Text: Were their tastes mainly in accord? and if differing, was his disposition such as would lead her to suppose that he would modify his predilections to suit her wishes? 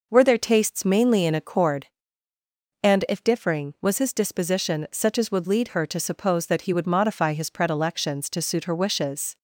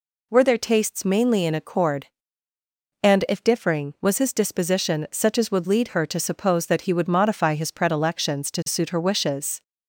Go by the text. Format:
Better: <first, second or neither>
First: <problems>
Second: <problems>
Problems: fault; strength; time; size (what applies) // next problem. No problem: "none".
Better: second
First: starts louder than the rest; noticeable; until 1.8 s; 5.5 dB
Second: none